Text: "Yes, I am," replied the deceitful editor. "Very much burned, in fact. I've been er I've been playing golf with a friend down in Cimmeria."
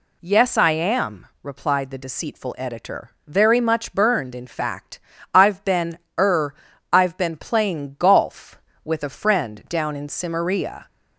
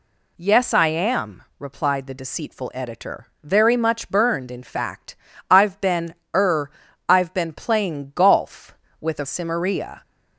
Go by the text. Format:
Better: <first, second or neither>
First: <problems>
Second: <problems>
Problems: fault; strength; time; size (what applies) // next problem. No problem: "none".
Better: first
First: pauses between "been" and "er"; slight; at 5.9 s; 0.22 s long // pauses between "er" and "I've"; at 6.5 s; 0.38 s long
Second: pauses between "been" and "er"; slight; at 6.1 s; 0.22 s long // pauses between "er" and "I've"; at 6.6 s; 0.38 s long // skips "friend down in"; at 9.2 s